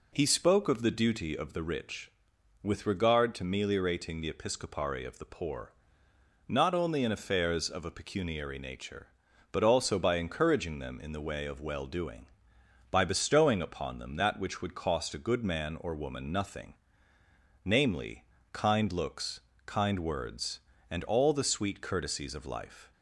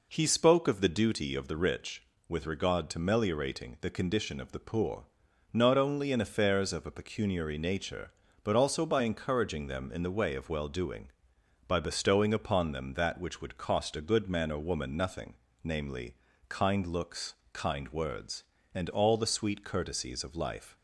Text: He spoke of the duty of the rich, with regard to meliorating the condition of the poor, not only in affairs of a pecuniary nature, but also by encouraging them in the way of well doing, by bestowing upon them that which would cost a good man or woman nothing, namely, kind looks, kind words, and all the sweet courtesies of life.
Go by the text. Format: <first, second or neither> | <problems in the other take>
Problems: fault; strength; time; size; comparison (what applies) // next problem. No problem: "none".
second | says "episcopari" for "condition"; at 4.3 s